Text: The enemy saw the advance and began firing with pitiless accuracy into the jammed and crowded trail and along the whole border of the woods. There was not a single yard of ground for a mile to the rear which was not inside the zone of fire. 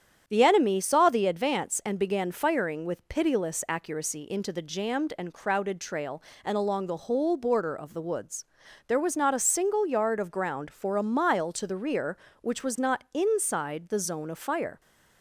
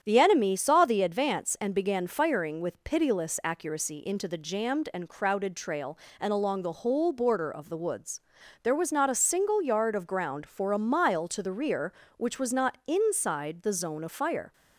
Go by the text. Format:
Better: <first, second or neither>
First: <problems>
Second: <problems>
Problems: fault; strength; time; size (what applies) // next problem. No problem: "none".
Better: neither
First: starts louder than the rest; strong; until 1.2 s; 8.5 dB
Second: starts louder than the rest; strong; until 1.0 s; 9 dB